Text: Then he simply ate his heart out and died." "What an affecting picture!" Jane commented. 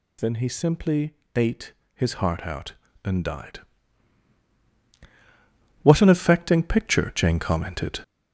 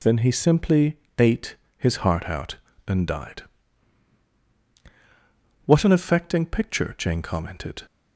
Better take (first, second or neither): second